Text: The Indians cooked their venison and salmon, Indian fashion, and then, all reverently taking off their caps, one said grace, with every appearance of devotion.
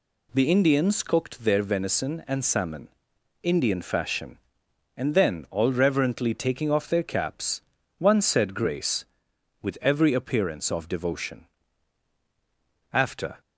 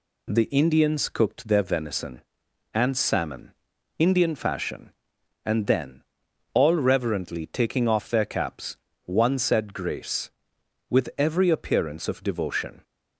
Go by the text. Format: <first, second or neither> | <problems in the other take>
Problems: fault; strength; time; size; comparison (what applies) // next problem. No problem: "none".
second | goes on to say "After"; slight; from 12.9 s on; 0.48 s long